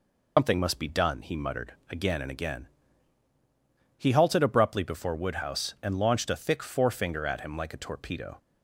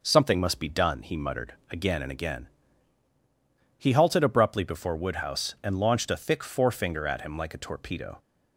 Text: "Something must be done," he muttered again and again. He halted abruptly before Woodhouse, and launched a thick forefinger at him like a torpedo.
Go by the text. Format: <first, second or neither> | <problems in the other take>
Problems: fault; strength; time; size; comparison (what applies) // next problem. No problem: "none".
second | loses the start of "Something"; at 0.3 s; 145 ms // pauses between "muttered" and "again"; slight; at 1.7 s; 0.16 s long; slight in the second